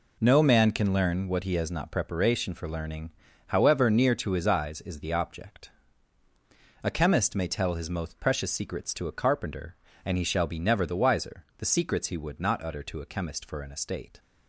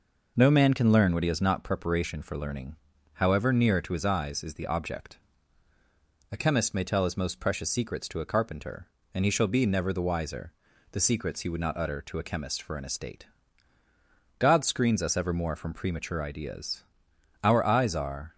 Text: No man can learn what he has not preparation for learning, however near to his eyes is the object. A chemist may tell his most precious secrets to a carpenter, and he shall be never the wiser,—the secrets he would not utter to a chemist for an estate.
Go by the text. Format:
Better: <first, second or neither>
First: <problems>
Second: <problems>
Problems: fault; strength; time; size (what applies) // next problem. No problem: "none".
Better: first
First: none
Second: goes on to say "God screens us evermore from premature ideas Our eyes are"; strong; from 14.3 s on; 3.9 s long